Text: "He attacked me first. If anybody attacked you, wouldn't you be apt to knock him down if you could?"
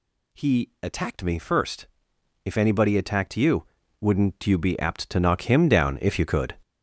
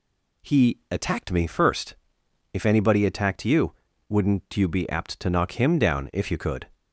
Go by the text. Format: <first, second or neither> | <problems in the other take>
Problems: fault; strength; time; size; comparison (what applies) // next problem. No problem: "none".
second | gets louder; strong; throughout; 9 dB